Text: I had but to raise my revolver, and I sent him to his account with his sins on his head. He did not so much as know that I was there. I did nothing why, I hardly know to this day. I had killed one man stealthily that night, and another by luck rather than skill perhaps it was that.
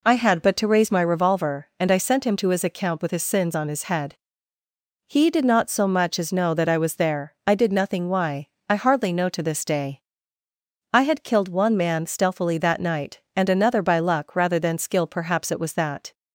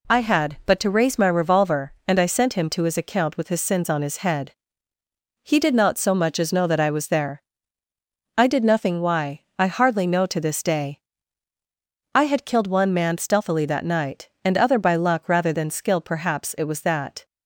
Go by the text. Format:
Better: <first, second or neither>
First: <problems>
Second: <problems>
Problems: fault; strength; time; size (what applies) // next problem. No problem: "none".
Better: first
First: none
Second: says "other" for "another"; at 14.5 s